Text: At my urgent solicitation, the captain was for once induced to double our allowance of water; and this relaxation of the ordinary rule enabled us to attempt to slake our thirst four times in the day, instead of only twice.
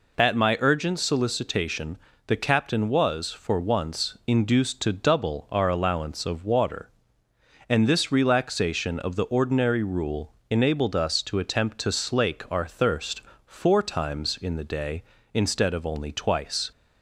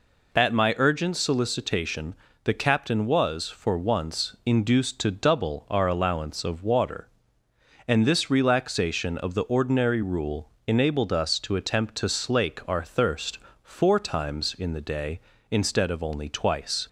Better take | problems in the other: neither | pauses between "rule" and "enabled"; slight; the same in both // pauses between "thirst" and "four"; slight; the same in both

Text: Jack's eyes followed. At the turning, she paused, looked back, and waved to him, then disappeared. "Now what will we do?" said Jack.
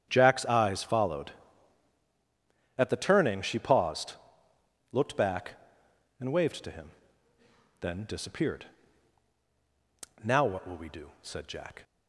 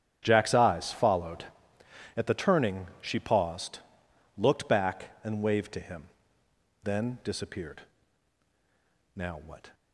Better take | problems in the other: first | starts louder than the rest; strong; until 1.2 s; 9.5 dB; strong in the first // stops before "will we do said Jack"; at 9.7 s

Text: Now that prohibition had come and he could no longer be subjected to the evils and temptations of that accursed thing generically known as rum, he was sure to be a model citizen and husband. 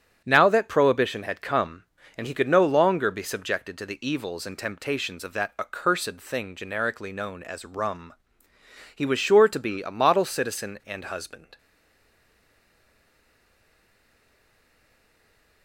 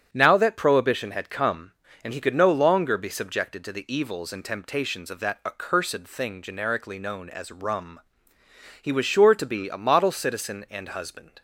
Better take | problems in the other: second | starts louder than the rest; strong; until 1.2 s; 7.5 dB; strong in the second // stays silent after the last word; strong; from 11.5 s on; 4.1 s long

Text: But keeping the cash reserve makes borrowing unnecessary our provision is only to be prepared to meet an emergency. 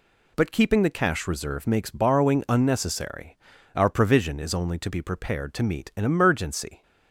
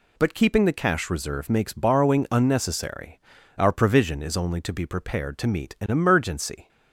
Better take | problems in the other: neither | pauses between "unnecessary" and "our"; slight; the same in both

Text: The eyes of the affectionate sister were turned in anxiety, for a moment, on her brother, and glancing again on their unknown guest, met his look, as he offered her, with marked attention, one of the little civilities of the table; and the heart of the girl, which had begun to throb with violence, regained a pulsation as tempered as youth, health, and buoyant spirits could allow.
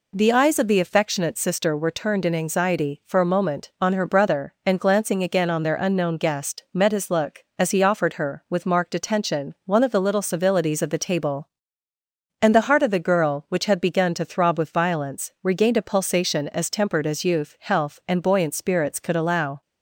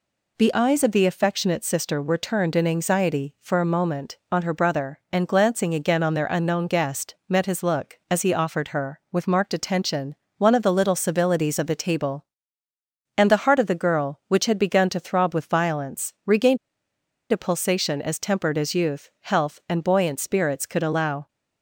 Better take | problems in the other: first | pauses between "regained" and "a"; noticeable; at 16.5 s; 0.73 s long

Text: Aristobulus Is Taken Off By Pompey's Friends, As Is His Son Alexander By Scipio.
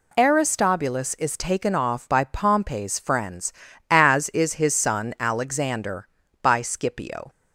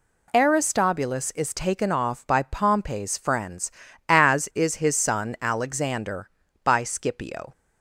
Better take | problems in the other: neither | none

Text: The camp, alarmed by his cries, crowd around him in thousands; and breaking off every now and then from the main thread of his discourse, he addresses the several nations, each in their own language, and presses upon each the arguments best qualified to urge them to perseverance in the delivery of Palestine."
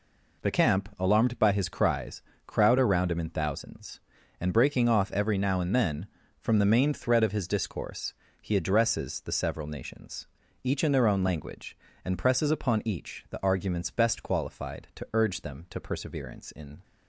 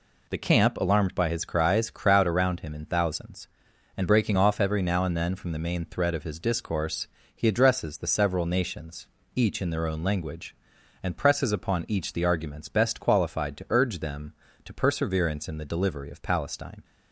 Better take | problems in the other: second | stops before "the delivery of Palestine"; at 16.8 s

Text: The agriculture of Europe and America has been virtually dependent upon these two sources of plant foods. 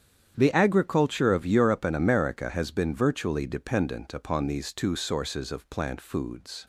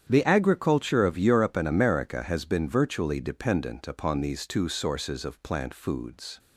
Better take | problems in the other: neither | starts louder than the rest; strong; the same in both

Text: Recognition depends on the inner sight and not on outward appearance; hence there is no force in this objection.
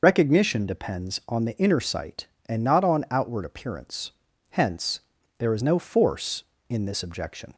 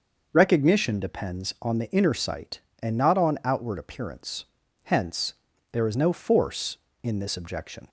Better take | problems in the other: second | loses the start of "Recognition"; at 0.0 s; 50 ms // pauses between "hence" and "there"; at 5.0 s; 0.38 s long; also in the second

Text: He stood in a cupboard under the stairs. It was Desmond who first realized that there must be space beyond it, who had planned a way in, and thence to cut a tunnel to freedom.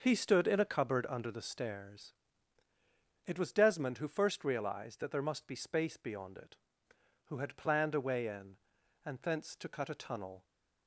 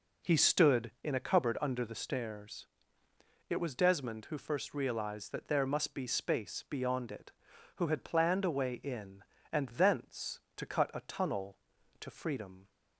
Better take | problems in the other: second | stops before "to freedom"; at 10.4 s

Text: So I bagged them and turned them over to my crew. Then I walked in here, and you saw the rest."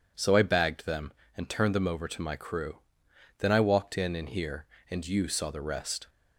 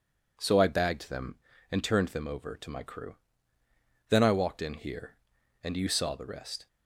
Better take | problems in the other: second | says "in" twice; at 4.1 s

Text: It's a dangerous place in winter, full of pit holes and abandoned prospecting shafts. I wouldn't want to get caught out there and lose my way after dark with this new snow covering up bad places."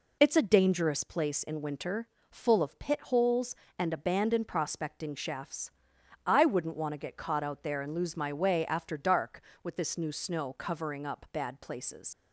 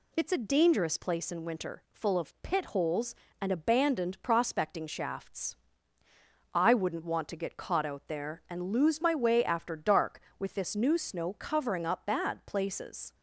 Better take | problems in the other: second | leaves "places" unfinished; at 12.1 s; 75 ms

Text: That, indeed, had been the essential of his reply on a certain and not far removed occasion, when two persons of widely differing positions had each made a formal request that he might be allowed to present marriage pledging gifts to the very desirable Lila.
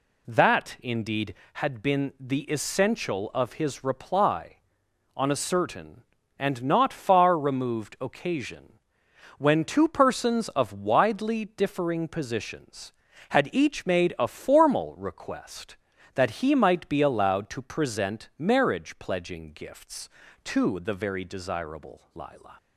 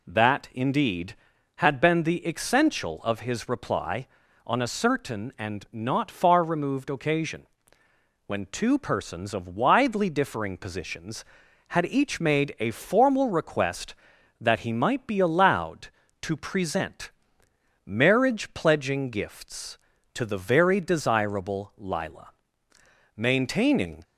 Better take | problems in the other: first | pauses between "present" and "marriage"; noticeable; at 17.1 s; 0.74 s long // goes on to say "Maintaining"; noticeable; from 23.1 s on; 0.88 s long

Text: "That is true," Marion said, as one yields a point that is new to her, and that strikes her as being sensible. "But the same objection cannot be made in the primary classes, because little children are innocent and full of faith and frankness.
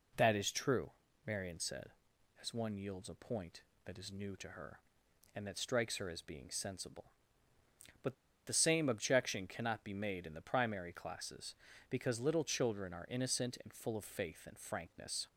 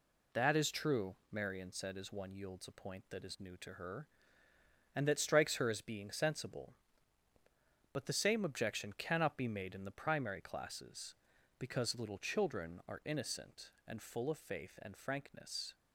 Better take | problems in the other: second | pauses between "But" and "the"; slight; at 8.1 s; 0.32 s long

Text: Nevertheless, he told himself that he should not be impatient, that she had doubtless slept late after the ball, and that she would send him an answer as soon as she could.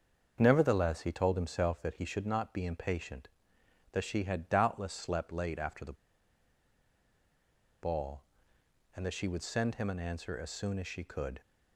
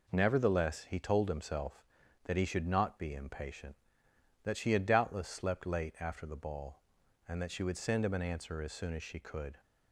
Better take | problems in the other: second | starts louder than the rest; until 1.4 s; 7 dB // pauses between "the" and "ball"; strong; at 5.9 s; 1.8 s long

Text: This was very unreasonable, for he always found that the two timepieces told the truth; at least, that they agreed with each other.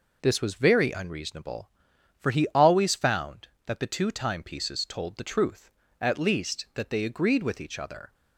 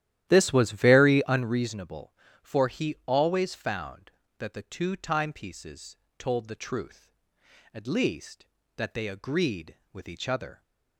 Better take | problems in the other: first | starts louder than the rest; strong; until 1.6 s; 12.5 dB // pauses between "timepieces" and "told"; slight; at 5.9 s; 0.22 s long

